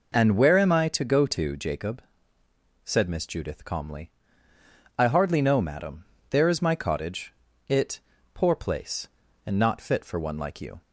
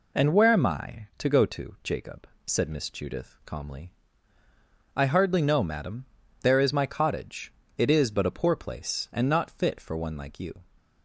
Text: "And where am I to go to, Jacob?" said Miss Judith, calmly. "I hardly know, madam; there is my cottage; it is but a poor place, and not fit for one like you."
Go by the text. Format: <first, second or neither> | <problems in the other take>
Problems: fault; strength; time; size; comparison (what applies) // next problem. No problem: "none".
second | skips "is but a"; at 8.1 s